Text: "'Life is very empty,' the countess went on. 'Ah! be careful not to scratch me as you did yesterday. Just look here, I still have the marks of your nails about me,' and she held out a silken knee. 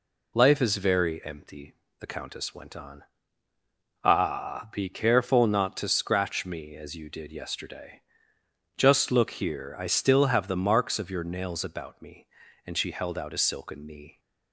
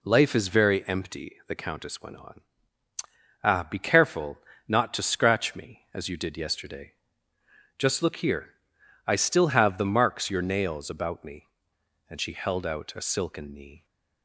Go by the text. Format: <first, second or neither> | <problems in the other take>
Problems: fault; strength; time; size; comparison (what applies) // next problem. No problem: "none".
first | pauses between "careful" and "not"; slight; at 4.3 s; 0.28 s long // skips "of"; at 10.3 s